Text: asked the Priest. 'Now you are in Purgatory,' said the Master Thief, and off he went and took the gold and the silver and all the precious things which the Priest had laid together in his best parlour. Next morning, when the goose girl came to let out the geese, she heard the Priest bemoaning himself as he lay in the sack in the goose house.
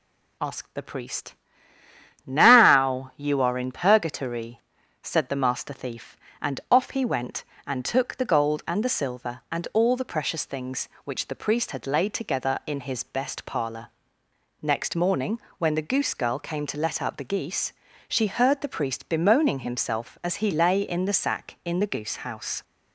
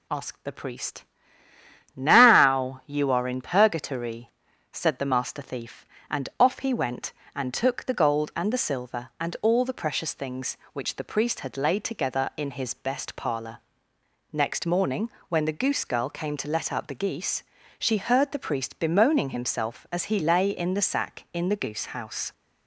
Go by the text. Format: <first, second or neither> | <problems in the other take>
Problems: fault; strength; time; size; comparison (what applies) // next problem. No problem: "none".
neither | none